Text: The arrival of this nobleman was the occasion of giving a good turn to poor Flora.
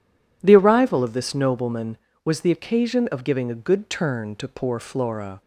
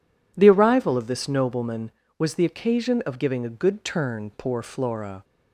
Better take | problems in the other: first | skips "to"; at 4.3 s

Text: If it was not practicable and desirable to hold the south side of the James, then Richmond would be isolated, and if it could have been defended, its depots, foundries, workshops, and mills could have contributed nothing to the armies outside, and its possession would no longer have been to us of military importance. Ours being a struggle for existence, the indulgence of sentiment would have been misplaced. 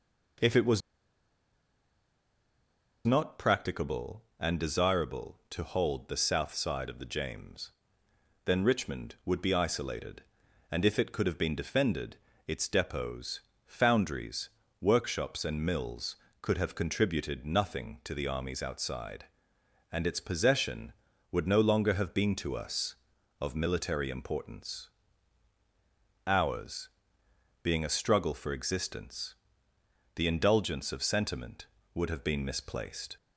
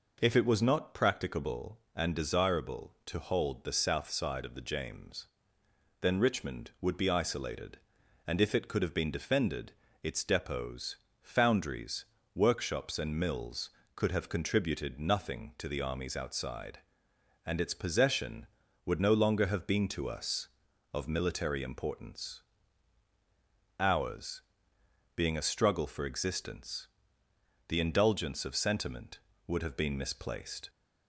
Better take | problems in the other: second | pauses between "was" and "not"; strong; at 0.8 s; 2.2 s long // pauses between "Ours" and "being"; noticeable; at 26.8 s; 0.74 s long; noticeable in the second

